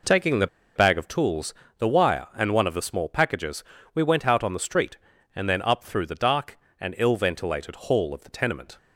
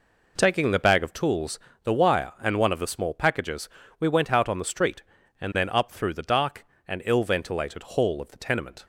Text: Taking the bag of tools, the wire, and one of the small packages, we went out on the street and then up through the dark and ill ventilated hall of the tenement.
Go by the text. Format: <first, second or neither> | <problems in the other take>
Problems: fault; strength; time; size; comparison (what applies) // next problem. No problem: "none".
second | pauses between "the" and "bag"; slight; at 0.4 s; 0.29 s long